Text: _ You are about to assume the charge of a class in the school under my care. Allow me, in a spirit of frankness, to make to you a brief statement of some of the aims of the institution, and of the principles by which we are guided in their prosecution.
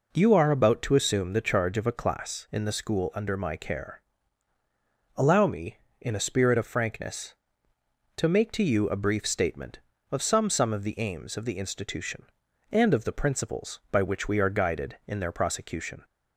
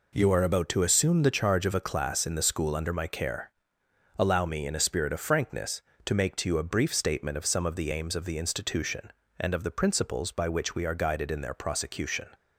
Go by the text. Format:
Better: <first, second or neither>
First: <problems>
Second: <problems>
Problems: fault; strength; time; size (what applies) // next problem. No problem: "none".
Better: second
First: says "some" twice; at 10.4 s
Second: none